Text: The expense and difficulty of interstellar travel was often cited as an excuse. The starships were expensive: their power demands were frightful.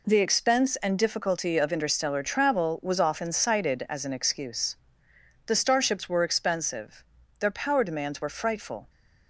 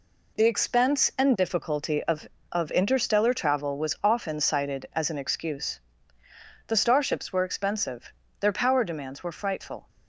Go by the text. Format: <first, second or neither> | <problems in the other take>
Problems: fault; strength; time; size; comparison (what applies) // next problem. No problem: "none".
first | says "of" twice; at 2.4 s